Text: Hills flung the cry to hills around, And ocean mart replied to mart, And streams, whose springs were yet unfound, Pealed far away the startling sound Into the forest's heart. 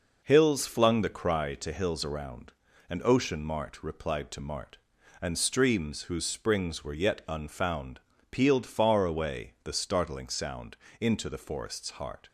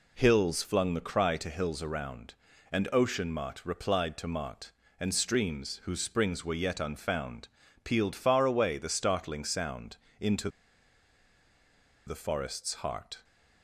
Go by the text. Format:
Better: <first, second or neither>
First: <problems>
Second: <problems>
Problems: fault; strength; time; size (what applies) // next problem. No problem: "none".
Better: first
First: pauses between "sound" and "Into"; slight; at 10.7 s; 0.24 s long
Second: pauses between "sound" and "Into"; slight; at 9.9 s; 0.20 s long // pauses between "Into" and "the"; strong; at 10.4 s; 1.5 s long